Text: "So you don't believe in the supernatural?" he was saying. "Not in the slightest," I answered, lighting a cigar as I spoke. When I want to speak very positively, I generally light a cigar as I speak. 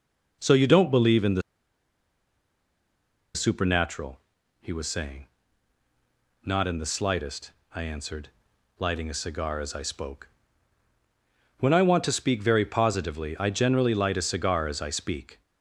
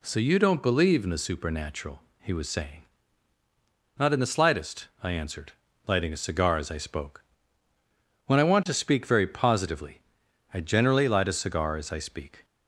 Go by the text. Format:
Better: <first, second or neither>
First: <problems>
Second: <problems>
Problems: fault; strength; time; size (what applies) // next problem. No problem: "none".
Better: second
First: pauses between "the" and "supernatural"; strong; at 1.4 s; 1.9 s long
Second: none